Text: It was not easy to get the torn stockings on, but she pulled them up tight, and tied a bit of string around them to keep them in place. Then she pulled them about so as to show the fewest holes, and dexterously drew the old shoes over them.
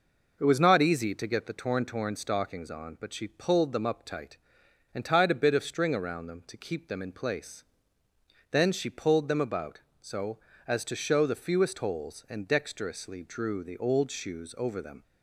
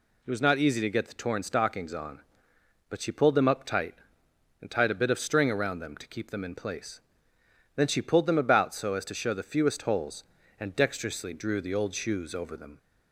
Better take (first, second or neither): second